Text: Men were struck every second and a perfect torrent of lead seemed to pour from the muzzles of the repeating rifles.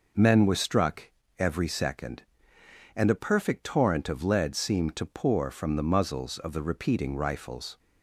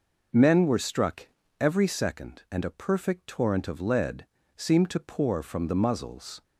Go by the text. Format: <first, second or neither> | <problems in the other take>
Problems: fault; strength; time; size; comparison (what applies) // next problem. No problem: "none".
first | pauses between "struck" and "every"; slight; at 1.2 s; 0.34 s long; slight in the first // pauses between "lead" and "seemed"; slight; at 4.2 s; 0.28 s long // stops before "of the repeating rifles"; at 6.4 s